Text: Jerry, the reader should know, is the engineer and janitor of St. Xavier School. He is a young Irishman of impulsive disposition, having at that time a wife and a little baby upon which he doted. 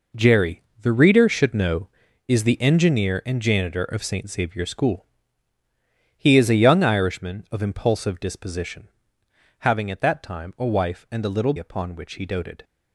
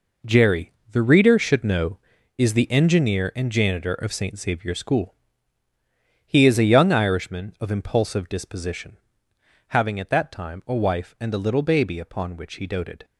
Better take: second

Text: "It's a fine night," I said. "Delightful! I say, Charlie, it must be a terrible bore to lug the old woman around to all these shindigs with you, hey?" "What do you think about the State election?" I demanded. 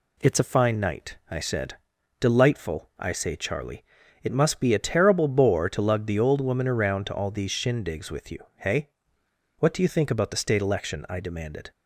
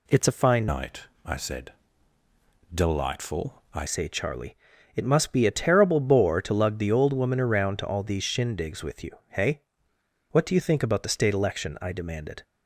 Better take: first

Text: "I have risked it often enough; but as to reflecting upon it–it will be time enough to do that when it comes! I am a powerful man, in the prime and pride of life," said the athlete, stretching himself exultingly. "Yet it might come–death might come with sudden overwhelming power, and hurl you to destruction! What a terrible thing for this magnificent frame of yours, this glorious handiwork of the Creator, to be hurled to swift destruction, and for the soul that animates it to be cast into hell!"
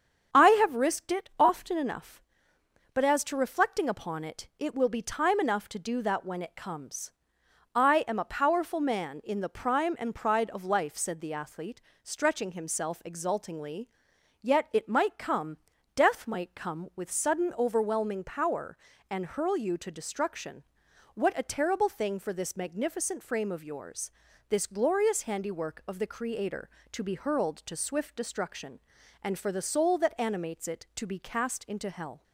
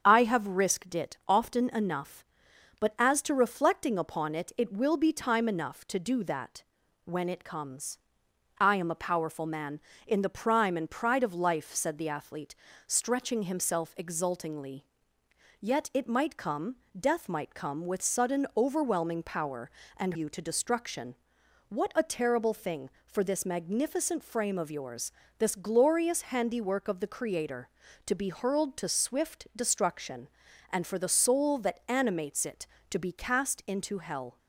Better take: first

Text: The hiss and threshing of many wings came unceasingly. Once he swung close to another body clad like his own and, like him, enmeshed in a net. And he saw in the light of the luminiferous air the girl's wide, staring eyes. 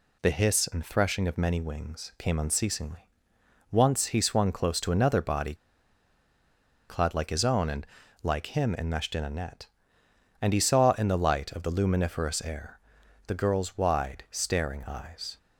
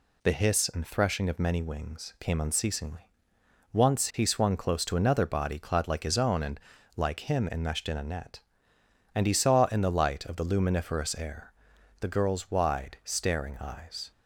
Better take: second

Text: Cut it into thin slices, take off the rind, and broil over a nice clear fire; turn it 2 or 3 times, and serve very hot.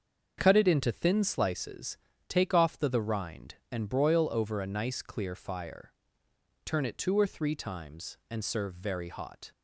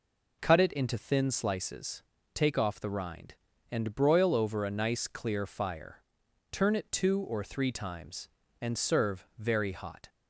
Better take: second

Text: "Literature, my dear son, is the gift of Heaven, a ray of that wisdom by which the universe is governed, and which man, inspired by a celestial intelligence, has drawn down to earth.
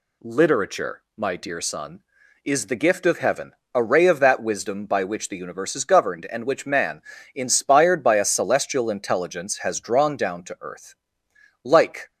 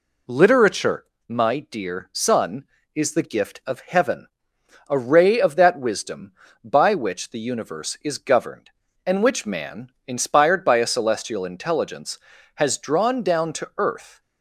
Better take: second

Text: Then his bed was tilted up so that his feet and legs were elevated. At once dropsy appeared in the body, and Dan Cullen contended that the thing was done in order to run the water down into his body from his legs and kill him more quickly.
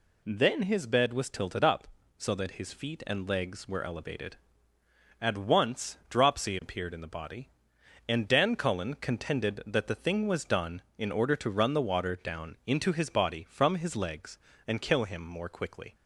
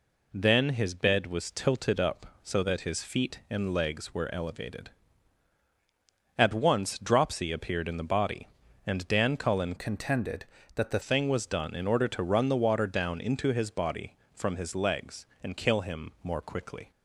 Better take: first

